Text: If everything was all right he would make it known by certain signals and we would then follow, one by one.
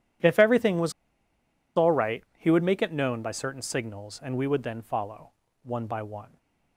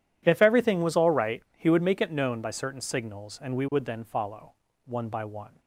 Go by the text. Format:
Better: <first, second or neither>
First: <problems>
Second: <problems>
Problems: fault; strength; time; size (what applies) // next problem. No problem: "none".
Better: second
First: pauses between "was" and "all"; noticeable; at 0.9 s; 0.84 s long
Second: none